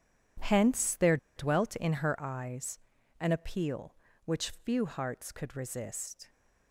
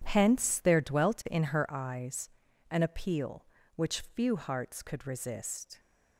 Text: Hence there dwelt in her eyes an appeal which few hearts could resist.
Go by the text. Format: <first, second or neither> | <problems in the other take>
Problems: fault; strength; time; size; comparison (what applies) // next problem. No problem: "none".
second | pauses between "there" and "dwelt"; slight; at 1.1 s; 0.19 s long // pauses between "eyes" and "an"; at 2.7 s; 0.40 s long; also in the second